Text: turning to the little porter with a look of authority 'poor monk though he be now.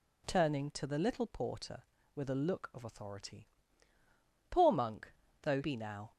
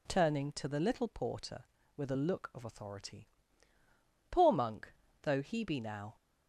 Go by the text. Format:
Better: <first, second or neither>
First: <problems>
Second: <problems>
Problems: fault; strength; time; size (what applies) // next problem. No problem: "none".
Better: second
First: pauses between "authority" and "poor"; at 3.4 s; 1.0 s long // pauses between "monk" and "though"; slight; at 5.1 s; 0.32 s long // skips "he"; at 5.6 s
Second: pauses between "authority" and "poor"; at 3.2 s; 1.0 s long // pauses between "monk" and "though"; slight; at 4.9 s; 0.32 s long